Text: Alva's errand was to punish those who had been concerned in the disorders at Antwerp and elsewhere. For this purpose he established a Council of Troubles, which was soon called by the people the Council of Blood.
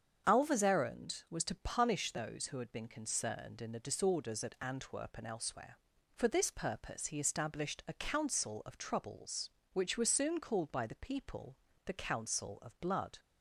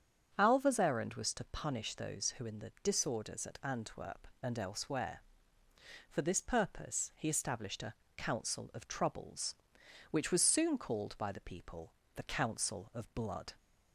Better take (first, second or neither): first